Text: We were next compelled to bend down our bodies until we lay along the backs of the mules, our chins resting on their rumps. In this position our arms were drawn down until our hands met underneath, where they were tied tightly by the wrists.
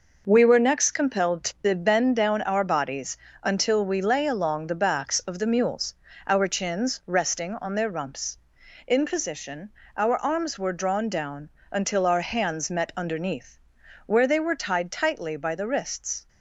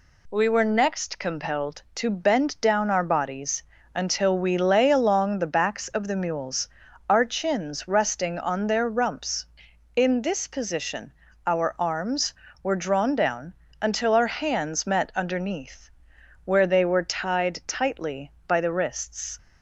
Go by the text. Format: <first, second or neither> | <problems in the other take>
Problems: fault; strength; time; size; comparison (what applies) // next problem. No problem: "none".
second | pauses between "bodies" and "until"; slight; at 3.1 s; 0.28 s long; slight in the second // skips "this"; at 9.0 s // pauses between "position" and "our"; slight; at 9.6 s; 0.26 s long; slight in the second // pauses between "down" and "until"; slight; at 11.5 s; 0.21 s long; slight in the second